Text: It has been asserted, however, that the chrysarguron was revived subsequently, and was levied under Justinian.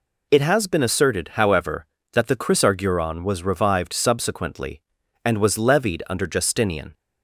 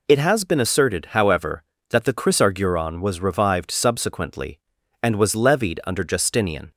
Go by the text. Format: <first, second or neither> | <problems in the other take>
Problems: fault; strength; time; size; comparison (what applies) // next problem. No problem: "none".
neither | none